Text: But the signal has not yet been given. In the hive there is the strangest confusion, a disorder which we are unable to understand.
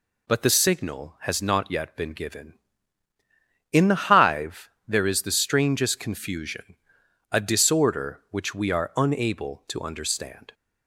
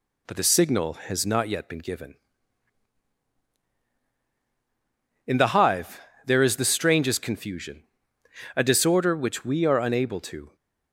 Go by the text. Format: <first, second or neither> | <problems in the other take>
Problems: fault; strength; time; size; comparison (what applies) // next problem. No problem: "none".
first | pauses between "hive" and "there"; slight; at 5.9 s; 0.26 s long; slight in the first // stops before "understand"; at 10.5 s